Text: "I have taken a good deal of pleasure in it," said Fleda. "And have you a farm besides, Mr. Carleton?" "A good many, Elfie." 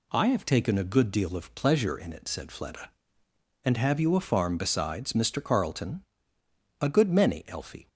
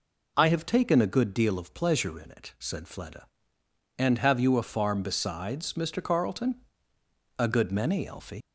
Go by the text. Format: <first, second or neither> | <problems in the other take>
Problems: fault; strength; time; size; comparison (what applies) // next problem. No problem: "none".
first | leaves "Elfie" unfinished; at 8.4 s; 95 ms